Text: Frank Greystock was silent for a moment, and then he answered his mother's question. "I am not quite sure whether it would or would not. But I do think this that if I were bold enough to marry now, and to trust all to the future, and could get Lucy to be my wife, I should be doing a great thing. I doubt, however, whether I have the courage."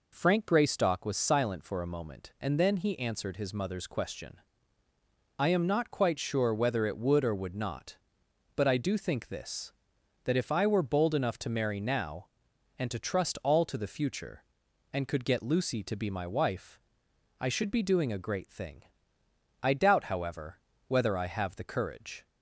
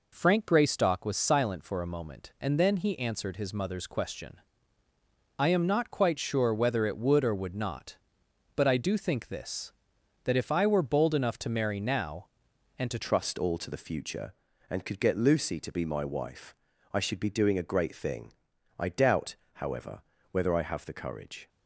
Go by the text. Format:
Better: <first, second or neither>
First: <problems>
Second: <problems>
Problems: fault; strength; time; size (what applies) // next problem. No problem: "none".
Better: first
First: none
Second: changes voice at "trust"; from 13.0 s on; 8.4 s long